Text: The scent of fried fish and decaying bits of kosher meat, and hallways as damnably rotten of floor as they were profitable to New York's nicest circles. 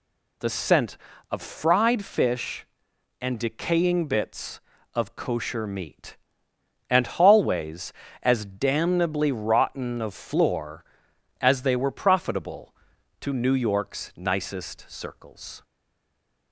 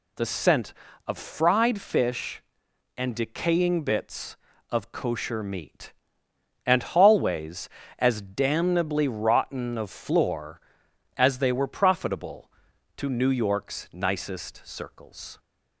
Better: second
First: stays silent after the last word; slight; from 15.6 s on; 0.9 s long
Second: none

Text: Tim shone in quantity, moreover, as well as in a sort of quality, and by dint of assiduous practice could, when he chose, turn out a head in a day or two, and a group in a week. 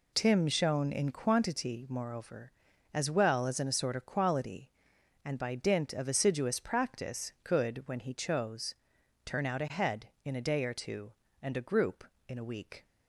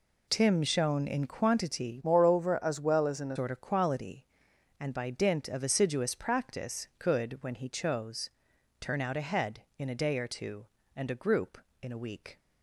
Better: first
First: none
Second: changes voice from "moreover" to "a"; from 2.0 to 3.3 s; 1.3 s long

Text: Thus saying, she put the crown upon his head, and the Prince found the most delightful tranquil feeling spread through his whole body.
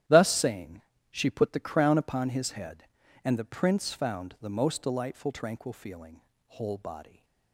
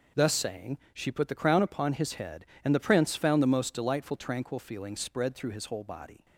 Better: second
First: starts louder than the rest; strong; until 1.3 s; 11.5 dB // skips "spread through his"; at 6.3 s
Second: none

